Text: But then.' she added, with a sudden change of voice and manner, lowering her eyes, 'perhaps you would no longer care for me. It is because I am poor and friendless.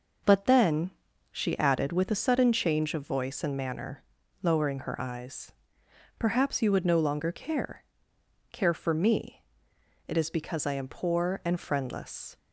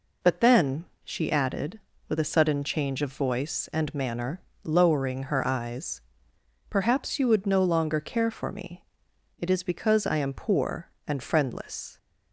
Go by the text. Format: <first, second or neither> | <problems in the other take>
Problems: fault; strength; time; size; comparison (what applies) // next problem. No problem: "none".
second | says "care" twice; at 8.5 s